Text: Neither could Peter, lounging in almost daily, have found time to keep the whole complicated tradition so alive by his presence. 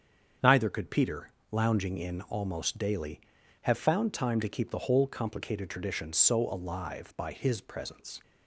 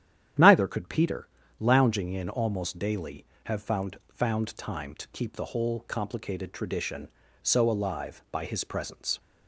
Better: first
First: starts louder than the rest; strong; until 1.6 s; 7.5 dB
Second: starts louder than the rest; strong; until 1.7 s; 10 dB // says "found" twice; at 4.1 s

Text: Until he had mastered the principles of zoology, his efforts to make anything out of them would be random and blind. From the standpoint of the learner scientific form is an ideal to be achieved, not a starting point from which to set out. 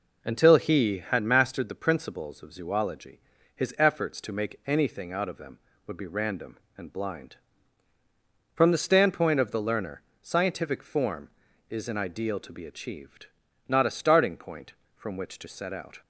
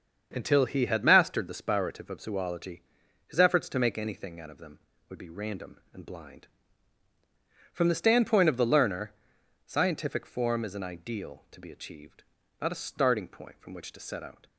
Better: first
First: pauses between "learner" and "scientific"; slight; at 10.0 s; 0.18 s long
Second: starts louder than the rest; until 1.3 s; 7 dB // says "spirative" for "principles"; at 1.6 s // pauses between "learner" and "scientific"; noticeable; at 9.1 s; 0.54 s long

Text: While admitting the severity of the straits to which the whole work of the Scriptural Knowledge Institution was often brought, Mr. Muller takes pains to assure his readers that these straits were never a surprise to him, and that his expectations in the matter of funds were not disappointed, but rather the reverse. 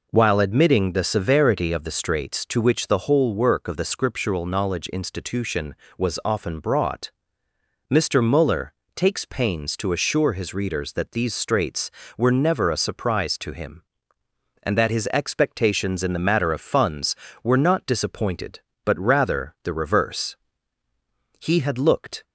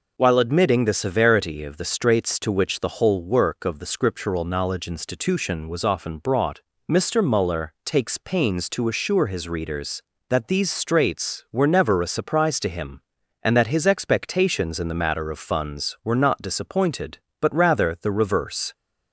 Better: second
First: pauses between "Muller" and "takes"; slight; at 8.7 s; 0.24 s long // goes on to say "He had looked"; noticeable; from 21.3 s on; 0.86 s long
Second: none

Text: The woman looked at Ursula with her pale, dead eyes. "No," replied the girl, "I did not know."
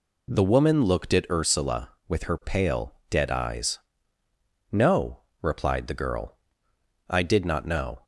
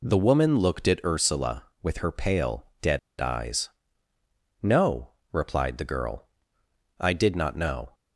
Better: first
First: none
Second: pauses between "dead" and "eyes"; slight; at 2.9 s; 0.20 s long

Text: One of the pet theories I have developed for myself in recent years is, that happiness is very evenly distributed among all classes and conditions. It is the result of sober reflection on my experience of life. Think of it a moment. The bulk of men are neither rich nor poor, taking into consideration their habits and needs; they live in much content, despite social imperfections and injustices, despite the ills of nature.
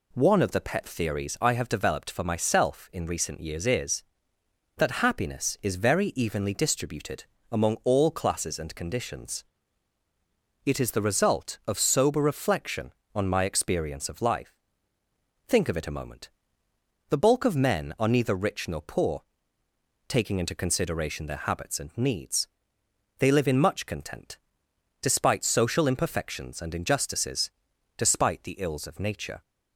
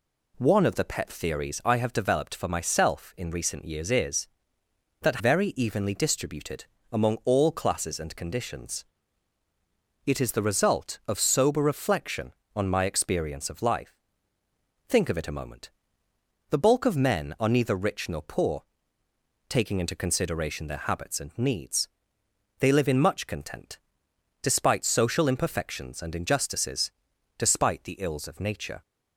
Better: first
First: pauses between "distributed" and "among"; slight; at 7.2 s; 0.26 s long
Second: skips "happiness is"; at 5.1 s // pauses between "distributed" and "among"; slight; at 6.6 s; 0.26 s long

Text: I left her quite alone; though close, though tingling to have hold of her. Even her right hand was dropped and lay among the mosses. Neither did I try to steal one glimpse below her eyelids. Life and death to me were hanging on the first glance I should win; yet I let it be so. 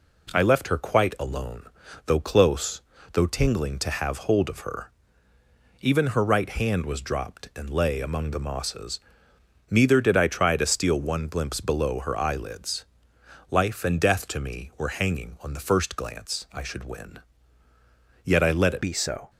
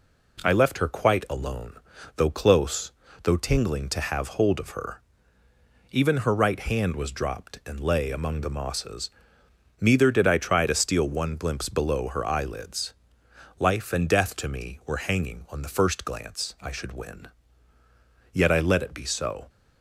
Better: second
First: changes voice at "be"; from 18.8 s on; 0.4 s long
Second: none

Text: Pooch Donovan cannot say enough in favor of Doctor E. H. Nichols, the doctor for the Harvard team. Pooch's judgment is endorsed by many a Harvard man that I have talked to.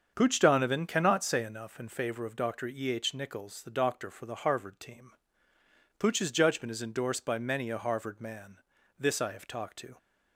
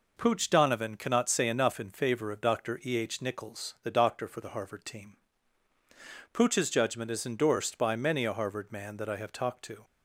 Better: second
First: starts louder than the rest; until 1.1 s; 7 dB // says "this" for "that"; at 8.9 s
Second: none

